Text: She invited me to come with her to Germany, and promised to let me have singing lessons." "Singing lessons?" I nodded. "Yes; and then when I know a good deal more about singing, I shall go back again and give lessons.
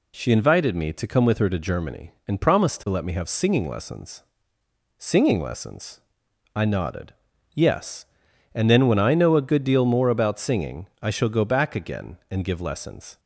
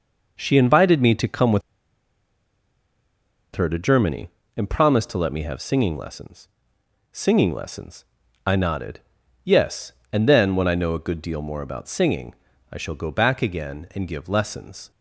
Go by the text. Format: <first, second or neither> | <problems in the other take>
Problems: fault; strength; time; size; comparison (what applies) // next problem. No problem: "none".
first | pauses between "with" and "her"; strong; at 1.6 s; 1.9 s long